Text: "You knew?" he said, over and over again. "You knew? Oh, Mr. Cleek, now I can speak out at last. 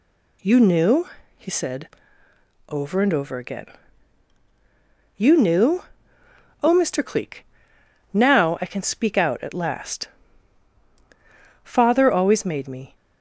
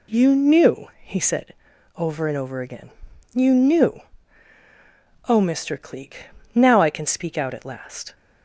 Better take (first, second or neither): second